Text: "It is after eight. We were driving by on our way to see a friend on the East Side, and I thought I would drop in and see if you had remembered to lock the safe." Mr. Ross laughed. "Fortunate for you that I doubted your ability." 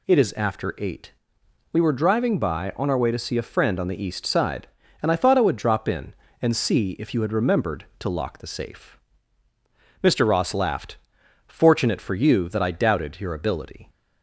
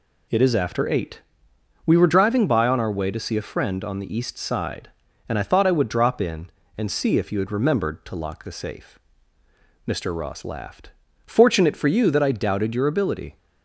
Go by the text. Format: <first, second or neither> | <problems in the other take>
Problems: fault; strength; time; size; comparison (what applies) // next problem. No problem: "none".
neither | none